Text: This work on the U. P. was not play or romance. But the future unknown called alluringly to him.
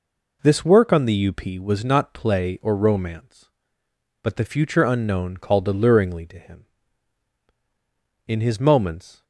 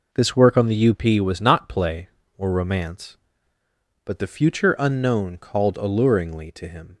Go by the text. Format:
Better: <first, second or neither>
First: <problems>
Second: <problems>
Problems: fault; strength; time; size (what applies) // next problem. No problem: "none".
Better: second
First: goes on to say "In his moments"; noticeable; from 8.2 s on; 0.98 s long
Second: none